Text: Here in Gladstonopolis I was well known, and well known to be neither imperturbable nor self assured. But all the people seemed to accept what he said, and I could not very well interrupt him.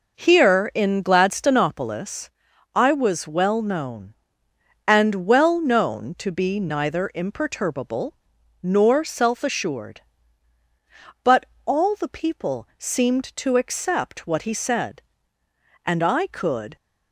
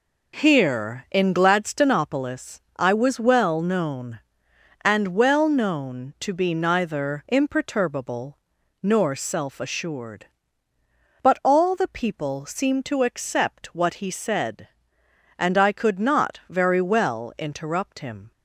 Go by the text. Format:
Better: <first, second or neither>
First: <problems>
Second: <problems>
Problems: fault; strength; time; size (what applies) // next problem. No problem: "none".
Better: second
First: pauses between "Gladstonopolis" and "I"; at 2.2 s; 0.44 s long // pauses between "imperturbable" and "nor"; at 8.1 s; 0.45 s long // pauses between "But" and "all"; slight; at 11.4 s; 0.18 s long // stops before "not very well interrupt him"; at 16.7 s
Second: pauses between "imperturbable" and "nor"; noticeable; at 8.3 s; 0.46 s long